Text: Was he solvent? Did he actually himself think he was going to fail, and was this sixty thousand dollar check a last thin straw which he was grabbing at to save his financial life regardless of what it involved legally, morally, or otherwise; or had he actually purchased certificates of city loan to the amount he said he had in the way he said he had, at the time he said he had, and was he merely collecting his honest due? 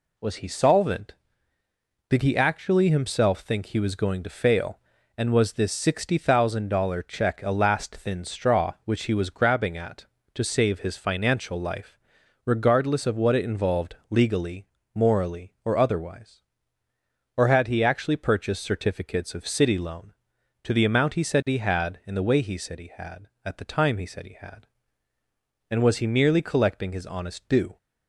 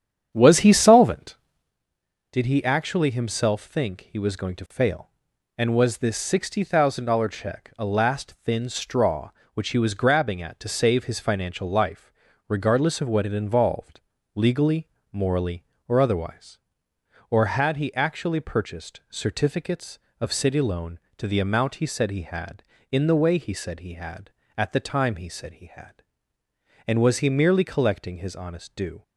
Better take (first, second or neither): first